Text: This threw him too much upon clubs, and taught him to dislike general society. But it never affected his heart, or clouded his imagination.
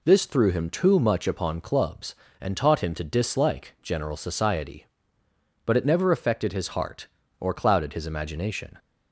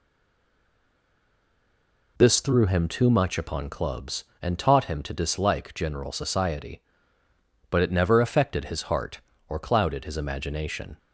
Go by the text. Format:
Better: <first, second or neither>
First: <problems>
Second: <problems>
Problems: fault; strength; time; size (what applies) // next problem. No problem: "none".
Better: first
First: none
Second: stays silent before the first word; until 2.1 s; 2.1 s long